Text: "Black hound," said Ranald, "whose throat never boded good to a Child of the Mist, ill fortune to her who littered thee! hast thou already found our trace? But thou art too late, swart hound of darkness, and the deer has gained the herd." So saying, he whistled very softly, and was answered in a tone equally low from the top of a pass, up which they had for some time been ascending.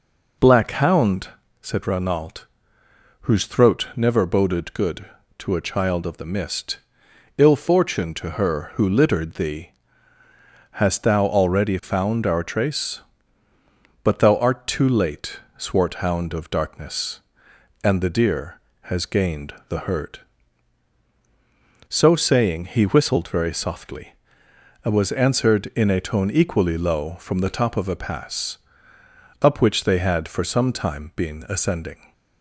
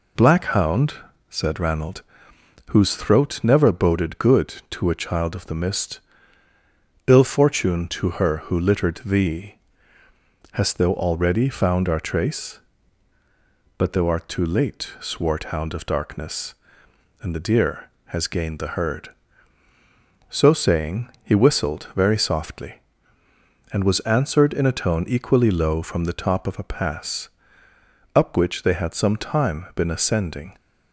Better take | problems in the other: first | skips "for"; at 28.9 s

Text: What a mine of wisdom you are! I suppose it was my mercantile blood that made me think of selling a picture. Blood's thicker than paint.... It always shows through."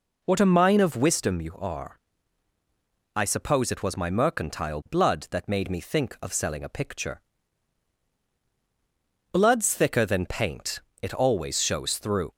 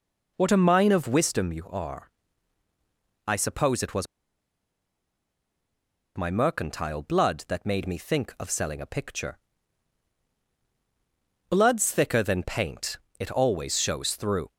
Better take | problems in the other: first | pauses between "was" and "my"; strong; at 4.0 s; 2.1 s long

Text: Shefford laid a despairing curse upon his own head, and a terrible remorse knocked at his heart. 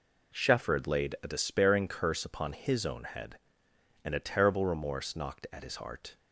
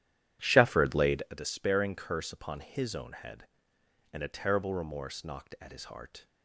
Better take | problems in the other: first | starts louder than the rest; strong; until 1.3 s; 11 dB

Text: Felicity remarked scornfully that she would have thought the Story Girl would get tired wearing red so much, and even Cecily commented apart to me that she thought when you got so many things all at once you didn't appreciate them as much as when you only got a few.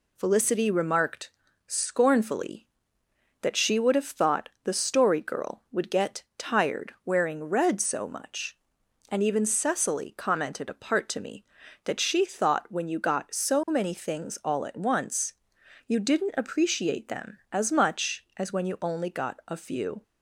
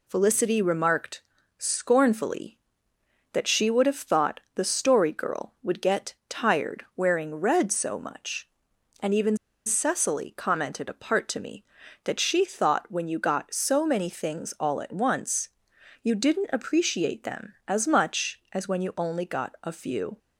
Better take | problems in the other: first | pauses between "remarked" and "scornfully"; slight; at 1.2 s; 0.36 s long; slight in the first // pauses between "thought" and "the"; slight; at 4.3 s; 0.16 s long; slight in the first // pauses between "get" and "tired"; slight; at 6.1 s; 0.16 s long; slight in the first // pauses between "even" and "Cecily"; slight; at 9.3 s; 0.30 s long // pauses between "once" and "you"; noticeable; at 15.4 s; 0.54 s long; noticeable in the first

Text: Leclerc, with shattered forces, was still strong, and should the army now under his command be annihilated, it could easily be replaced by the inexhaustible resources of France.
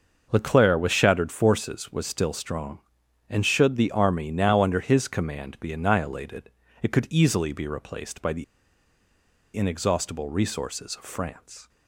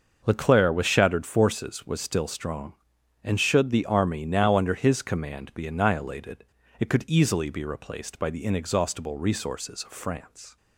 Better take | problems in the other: second | starts louder than the rest; until 1.3 s; 6 dB; also in the second // pauses between "the" and "inexhaustible"; at 8.4 s; 1.1 s long

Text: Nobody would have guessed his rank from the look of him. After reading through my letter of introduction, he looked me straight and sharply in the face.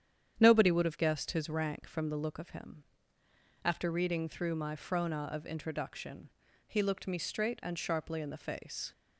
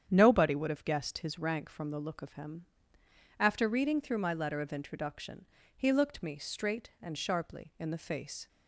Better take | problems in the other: second | starts louder than the rest; strong; until 1.3 s; 9 dB; strong in the second // says "frona" for "letter"; at 4.7 s

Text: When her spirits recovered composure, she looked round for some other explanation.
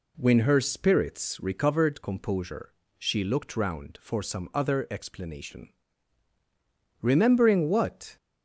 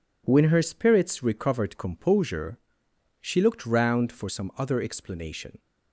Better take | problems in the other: second | goes on to say "Remembering what"; noticeable; from 7.0 s on; 1.1 s long

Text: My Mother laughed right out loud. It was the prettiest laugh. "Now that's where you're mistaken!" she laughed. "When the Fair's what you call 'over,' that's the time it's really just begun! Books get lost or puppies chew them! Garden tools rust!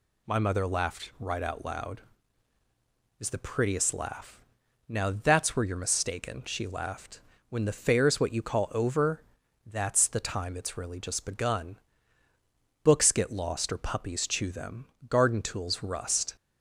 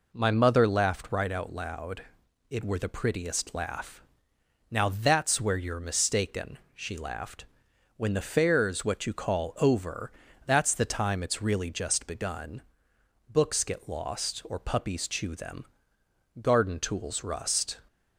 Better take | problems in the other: first | says "were" for "was"; at 2.6 s

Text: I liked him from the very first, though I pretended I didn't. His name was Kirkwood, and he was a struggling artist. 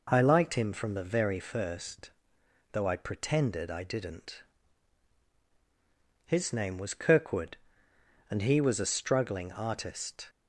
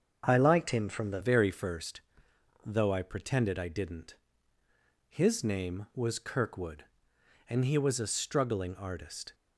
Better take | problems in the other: first | starts louder than the rest; until 1.2 s; 7 dB // changes voice at "very"; from 1.2 s on; 8.1 s long

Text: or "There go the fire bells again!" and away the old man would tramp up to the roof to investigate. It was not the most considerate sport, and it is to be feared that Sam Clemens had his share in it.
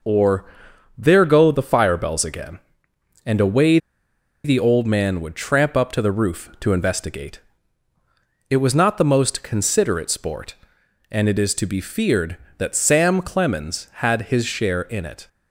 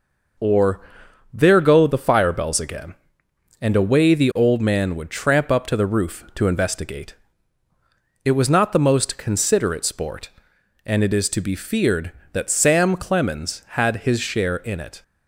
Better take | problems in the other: second | pauses between "or" and "There"; noticeable; at 0.4 s; 0.48 s long; noticeable in the second // pauses between "away" and "the"; noticeable; at 3.7 s; 0.66 s long

